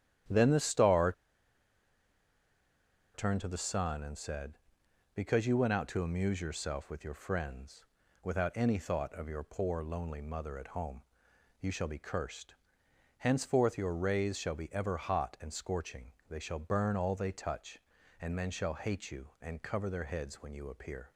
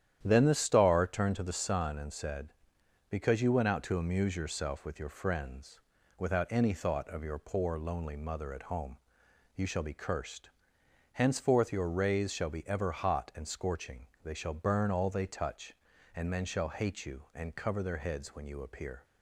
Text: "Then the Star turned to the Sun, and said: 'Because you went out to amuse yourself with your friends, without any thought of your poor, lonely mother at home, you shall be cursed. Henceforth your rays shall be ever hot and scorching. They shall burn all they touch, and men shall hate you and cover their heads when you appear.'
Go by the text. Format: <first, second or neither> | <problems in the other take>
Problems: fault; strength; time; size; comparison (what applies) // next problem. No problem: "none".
second | starts louder than the rest; strong; until 3.3 s; 10.5 dB; strong in the second // pauses between "Star" and "turned"; strong; at 1.1 s; 2.0 s long